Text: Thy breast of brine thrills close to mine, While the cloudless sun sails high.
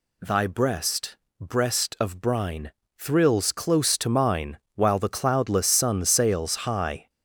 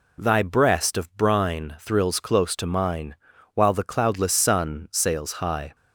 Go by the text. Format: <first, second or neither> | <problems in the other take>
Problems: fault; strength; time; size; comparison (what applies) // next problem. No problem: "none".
second | says "breast" twice; at 1.3 s // pauses between "brine" and "thrills"; slight; at 2.7 s; 0.28 s long